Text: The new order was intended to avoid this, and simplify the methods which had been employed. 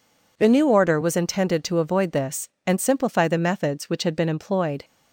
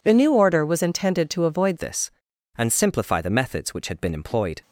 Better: first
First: none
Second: changes voice at "this"; from 1.7 s on; 2.9 s long

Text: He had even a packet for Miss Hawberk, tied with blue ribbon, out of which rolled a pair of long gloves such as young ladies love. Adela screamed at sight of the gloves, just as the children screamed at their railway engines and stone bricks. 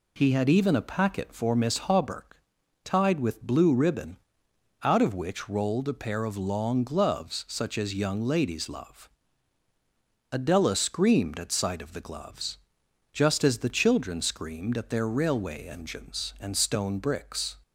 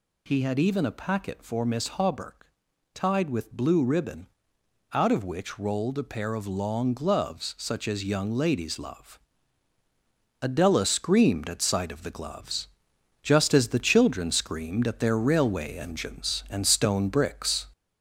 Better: first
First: none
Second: gets louder; noticeable; throughout; 4 dB

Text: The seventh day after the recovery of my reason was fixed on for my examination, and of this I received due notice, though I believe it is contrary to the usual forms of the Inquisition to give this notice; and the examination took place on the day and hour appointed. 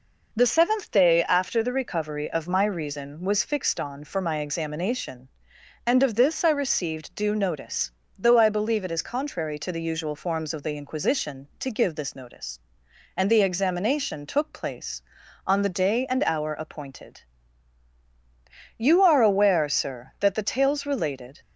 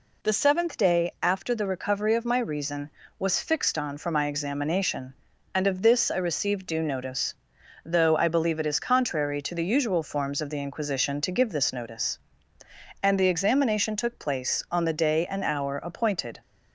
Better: second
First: goes on to say "You are aware Sir that the tales related"; strong; from 18.7 s on; 2.6 s long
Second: none

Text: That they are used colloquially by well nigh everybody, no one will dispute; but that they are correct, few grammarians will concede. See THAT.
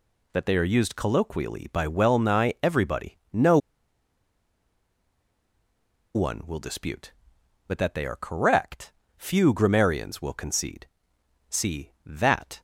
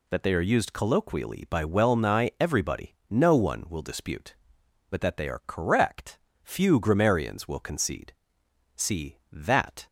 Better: second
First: pauses between "no" and "one"; strong; at 3.5 s; 2.5 s long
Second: none

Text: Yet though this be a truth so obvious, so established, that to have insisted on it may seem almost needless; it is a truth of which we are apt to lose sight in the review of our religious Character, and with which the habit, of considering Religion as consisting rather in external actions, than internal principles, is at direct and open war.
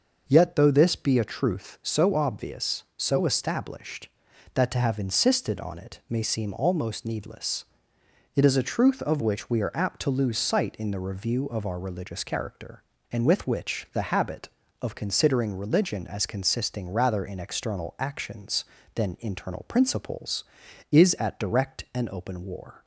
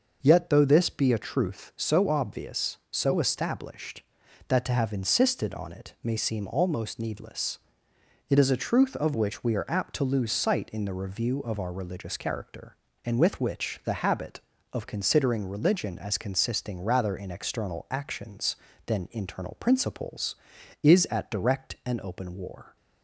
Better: neither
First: none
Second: none

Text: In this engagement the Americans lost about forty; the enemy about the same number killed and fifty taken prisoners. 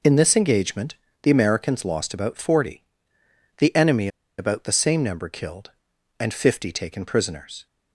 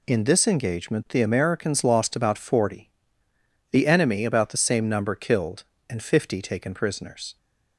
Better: second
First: pauses between "engagement" and "the"; slight; at 0.9 s; 0.26 s long // pauses between "enemy" and "about"; slight; at 4.0 s; 0.30 s long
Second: none

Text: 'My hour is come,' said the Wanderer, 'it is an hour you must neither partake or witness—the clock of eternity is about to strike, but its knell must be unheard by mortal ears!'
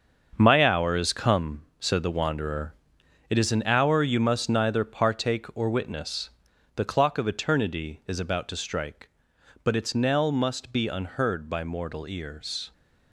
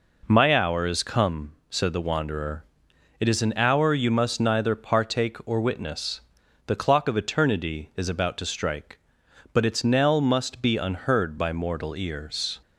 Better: second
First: gets quieter; strong; throughout; 9.5 dB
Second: none

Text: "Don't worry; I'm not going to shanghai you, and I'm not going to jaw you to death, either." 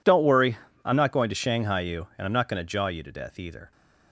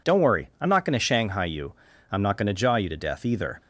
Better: first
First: none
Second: skips "and"; at 1.9 s

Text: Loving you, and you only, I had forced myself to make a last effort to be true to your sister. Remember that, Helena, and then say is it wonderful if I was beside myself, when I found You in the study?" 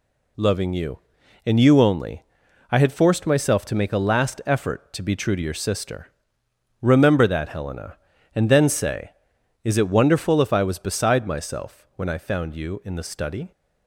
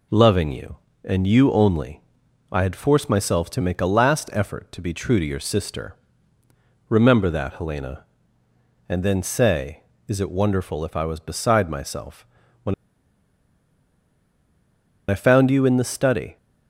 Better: first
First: none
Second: pauses between "when" and "I"; strong; at 12.7 s; 2.3 s long

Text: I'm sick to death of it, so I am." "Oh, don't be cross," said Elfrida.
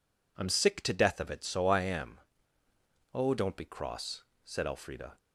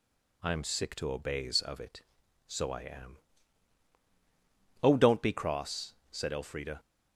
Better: first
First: none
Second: says "obeys" for "death"; at 1.1 s

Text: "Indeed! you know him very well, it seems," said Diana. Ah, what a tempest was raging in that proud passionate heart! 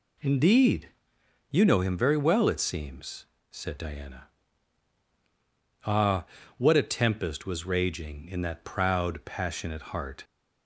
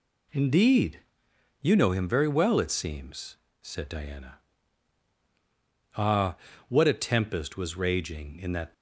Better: first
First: none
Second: stops before "proud passionate heart"; at 8.7 s

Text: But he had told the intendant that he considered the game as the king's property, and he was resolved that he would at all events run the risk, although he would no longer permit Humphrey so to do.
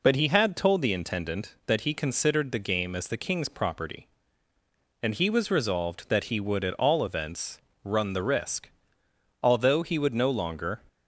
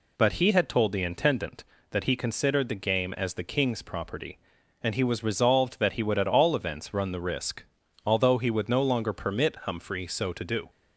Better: second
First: pauses between "events" and "run"; slight; at 7.5 s; 0.26 s long // stops before "permit Humphrey so to do"; at 10.8 s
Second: none

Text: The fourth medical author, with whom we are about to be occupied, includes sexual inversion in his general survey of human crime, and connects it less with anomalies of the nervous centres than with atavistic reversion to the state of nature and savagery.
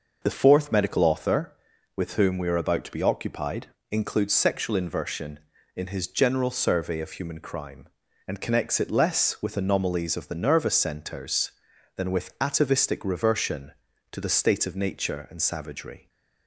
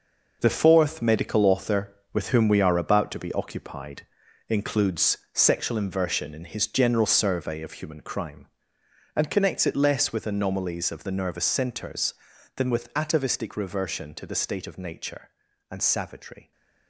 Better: first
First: none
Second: gets quieter; strong; throughout; 9 dB // pauses between "includes" and "sexual"; slight; at 5.1 s; 0.16 s long

